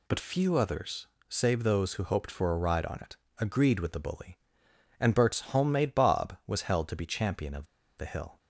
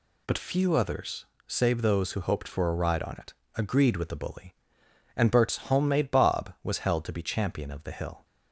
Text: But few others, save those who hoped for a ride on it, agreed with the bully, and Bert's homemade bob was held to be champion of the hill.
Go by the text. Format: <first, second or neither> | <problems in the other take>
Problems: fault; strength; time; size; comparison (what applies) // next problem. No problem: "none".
second | pauses between "of" and "the"; slight; at 7.6 s; 0.31 s long